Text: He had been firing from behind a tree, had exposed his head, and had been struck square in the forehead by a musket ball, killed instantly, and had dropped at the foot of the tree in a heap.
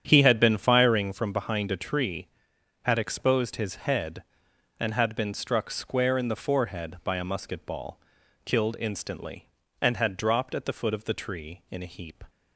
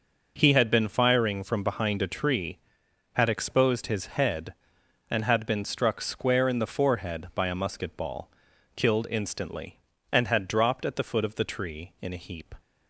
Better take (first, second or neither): second